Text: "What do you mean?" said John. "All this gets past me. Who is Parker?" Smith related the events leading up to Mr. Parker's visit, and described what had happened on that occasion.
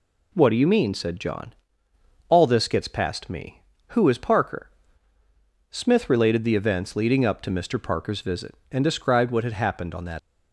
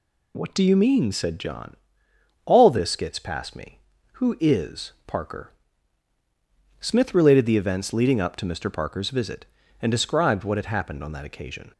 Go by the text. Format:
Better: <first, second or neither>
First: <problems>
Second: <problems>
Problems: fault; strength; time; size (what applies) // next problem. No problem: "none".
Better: second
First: stops before "occasion"; at 10.1 s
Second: none